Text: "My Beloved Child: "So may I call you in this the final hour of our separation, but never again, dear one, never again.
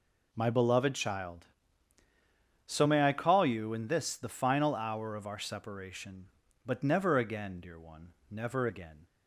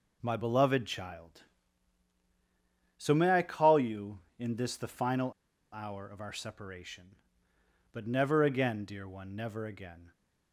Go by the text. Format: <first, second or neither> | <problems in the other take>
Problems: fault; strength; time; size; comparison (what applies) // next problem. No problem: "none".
first | pauses between "final" and "hour"; at 5.3 s; 0.39 s long